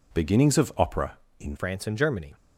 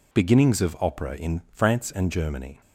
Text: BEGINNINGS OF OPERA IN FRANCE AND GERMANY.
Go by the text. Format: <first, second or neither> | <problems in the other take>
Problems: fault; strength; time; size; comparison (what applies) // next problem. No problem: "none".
second | changes voice at "FRANCE"; from 1.5 s on; 0.8 s long